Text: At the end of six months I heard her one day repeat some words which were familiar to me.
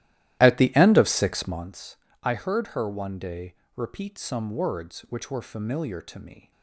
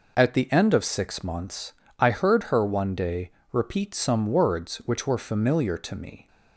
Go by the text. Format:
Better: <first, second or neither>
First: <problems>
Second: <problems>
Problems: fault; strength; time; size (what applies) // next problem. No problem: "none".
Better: second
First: starts louder than the rest; strong; until 1.7 s; 14.5 dB // pauses between "months" and "I"; slight; at 1.9 s; 0.26 s long // pauses between "day" and "repeat"; slight; at 3.5 s; 0.22 s long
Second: pauses between "months" and "I"; slight; at 1.7 s; 0.26 s long // pauses between "day" and "repeat"; slight; at 3.3 s; 0.22 s long